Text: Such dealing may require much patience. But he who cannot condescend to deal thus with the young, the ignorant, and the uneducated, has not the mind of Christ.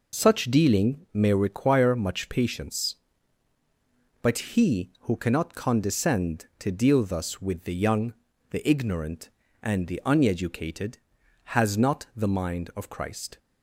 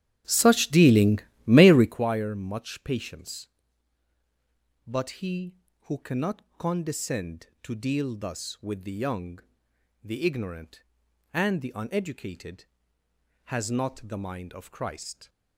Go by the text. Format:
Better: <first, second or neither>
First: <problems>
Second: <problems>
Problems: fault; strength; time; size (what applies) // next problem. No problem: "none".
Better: first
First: none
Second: starts louder than the rest; strong; until 2.1 s; 11 dB // pauses between "dealing" and "may"; slight; at 1.1 s; 0.26 s long // pauses between "cannot" and "condescend"; slight; at 6.4 s; 0.16 s long